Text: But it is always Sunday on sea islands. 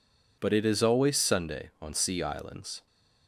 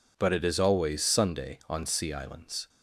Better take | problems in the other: neither | none

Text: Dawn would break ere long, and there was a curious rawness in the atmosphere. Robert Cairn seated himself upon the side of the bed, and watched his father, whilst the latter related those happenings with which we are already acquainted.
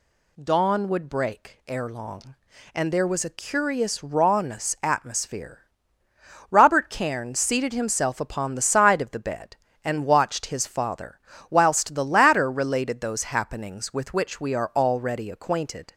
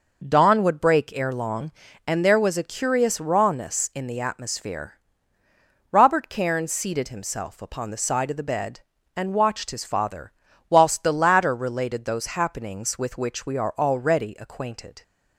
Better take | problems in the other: second | skips "in the"; at 4.7 s

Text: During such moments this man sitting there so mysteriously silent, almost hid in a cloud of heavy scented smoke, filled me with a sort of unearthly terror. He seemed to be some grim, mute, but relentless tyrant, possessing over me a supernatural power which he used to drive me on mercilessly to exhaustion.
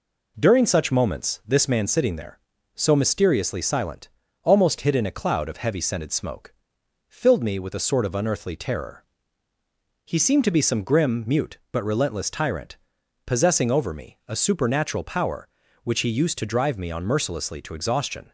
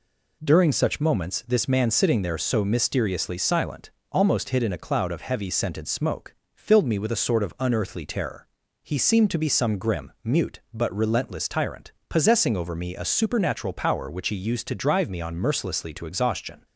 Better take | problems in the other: neither | none

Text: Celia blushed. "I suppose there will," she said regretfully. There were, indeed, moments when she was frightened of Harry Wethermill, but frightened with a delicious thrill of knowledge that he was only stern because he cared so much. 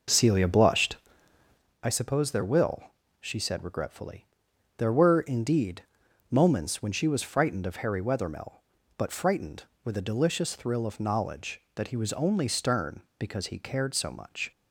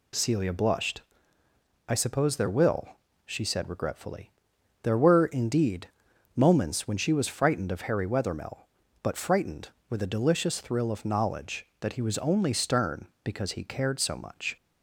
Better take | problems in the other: second | starts louder than the rest; noticeable; until 1.7 s; 5.5 dB

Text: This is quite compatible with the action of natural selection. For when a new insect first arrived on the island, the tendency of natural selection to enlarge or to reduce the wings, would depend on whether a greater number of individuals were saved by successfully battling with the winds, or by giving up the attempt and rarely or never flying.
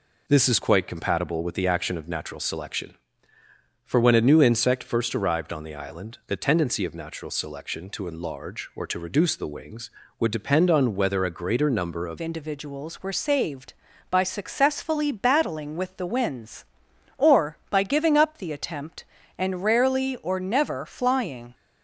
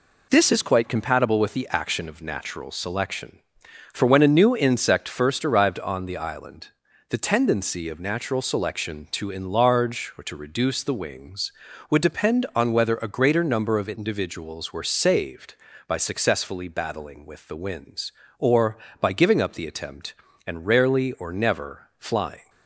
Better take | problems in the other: second | changes voice at "individuals"; from 12.1 s on; 9.4 s long

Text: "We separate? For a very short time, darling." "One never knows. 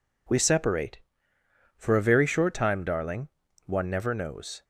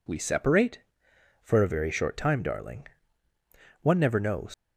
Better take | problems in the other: first | leaves "knows" unfinished; at 4.5 s; 115 ms

